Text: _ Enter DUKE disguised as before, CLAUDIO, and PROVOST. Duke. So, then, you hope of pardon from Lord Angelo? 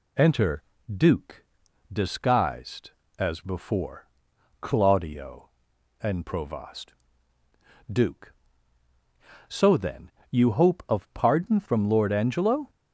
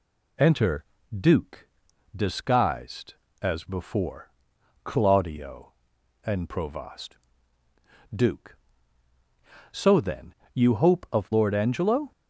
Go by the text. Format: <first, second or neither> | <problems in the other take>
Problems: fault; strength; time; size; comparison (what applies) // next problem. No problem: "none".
first | pauses between "Enter" and "DUKE"; slight; at 0.8 s; 0.34 s long; slight in the first // pauses between "DUKE" and "disguised"; noticeable; at 1.6 s; 0.48 s long; noticeable in the first // skips "pardon from"; at 11.3 s